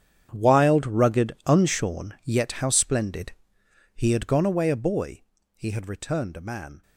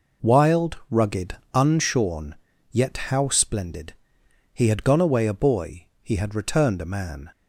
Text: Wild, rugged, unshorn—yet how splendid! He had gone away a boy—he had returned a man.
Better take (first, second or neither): second